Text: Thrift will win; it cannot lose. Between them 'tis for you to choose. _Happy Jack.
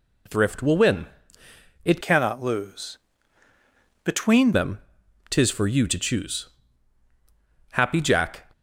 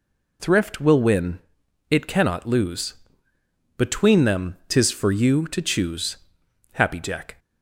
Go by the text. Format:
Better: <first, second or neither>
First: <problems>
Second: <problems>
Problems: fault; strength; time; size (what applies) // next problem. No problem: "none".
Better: second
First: changes voice from "cannot" to "Between"; from 2.0 to 4.5 s; 2.5 s long // pauses between "them" and "tis"; noticeable; at 4.7 s; 0.50 s long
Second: none